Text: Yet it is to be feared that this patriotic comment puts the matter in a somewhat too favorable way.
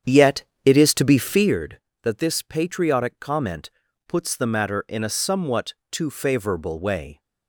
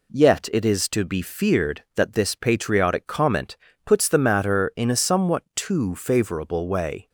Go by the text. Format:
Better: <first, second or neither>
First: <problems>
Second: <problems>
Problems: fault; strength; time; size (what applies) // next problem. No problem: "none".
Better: second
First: starts louder than the rest; strong; until 1.6 s; 8.5 dB // pauses between "Yet" and "it"; slight; at 0.4 s; 0.22 s long // pauses between "comment" and "puts"; at 3.6 s; 0.38 s long // pauses between "somewhat" and "too"; slight; at 5.7 s; 0.18 s long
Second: pauses between "comment" and "puts"; slight; at 3.5 s; 0.28 s long